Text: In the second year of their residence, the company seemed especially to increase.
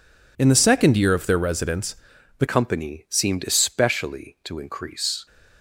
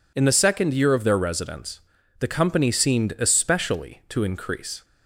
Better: second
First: changes voice at "company"; from 2.4 s on; 2.8 s long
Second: none

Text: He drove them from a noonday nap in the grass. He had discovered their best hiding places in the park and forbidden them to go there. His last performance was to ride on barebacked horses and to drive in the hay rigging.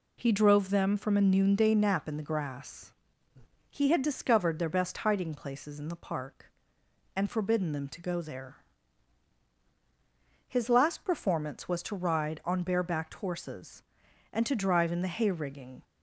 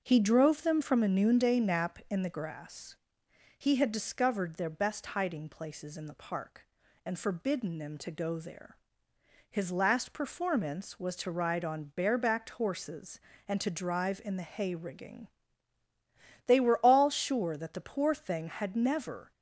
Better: first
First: none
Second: starts louder than the rest; noticeable; until 1.0 s; 6 dB // goes on to say "They were all sure that the poor thing had never"; strong; from 16.4 s on; 2.8 s long

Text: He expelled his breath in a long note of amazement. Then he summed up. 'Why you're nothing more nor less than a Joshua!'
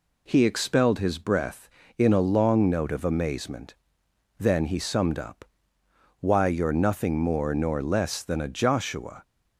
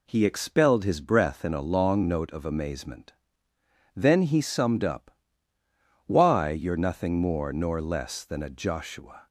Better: neither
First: none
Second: none

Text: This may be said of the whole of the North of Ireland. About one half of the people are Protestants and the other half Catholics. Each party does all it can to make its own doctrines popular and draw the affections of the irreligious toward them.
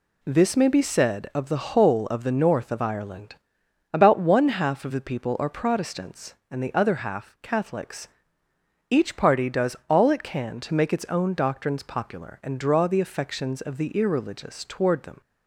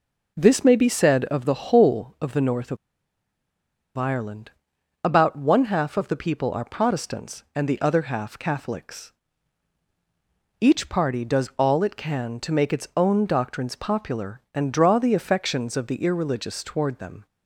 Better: first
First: none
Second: pauses between "of" and "Ireland"; at 2.7 s; 1.2 s long

